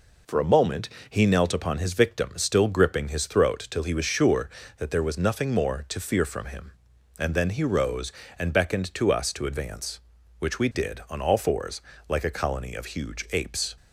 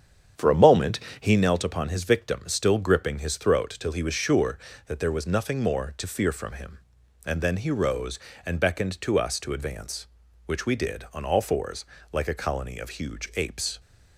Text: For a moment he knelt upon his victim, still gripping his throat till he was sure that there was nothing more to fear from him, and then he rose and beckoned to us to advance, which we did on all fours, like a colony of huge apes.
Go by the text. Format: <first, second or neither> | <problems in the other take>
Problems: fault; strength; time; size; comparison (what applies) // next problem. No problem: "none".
first | starts louder than the rest; strong; until 1.4 s; 8.5 dB // pauses between "moment" and "he"; slight; at 0.9 s; 0.20 s long; slight in the first